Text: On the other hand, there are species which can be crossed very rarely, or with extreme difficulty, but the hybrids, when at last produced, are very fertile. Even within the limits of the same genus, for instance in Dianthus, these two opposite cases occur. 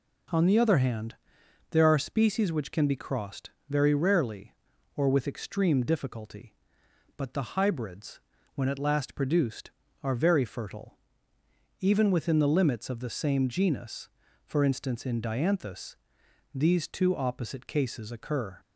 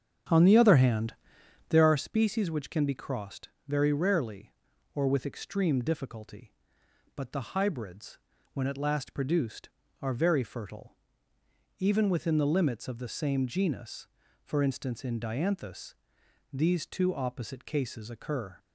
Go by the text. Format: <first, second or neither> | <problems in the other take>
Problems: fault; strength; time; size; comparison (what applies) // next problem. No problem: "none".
first | starts louder than the rest; strong; until 2.0 s; 8.5 dB // pauses between "crossed" and "very"; slight; at 3.4 s; 0.20 s long; slight in the first